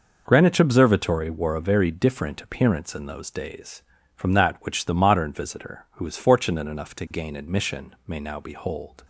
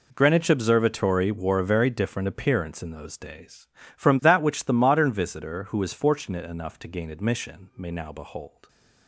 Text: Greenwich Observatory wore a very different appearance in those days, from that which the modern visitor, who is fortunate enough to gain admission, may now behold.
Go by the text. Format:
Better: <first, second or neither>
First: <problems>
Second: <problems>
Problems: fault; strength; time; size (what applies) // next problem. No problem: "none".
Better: neither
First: none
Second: none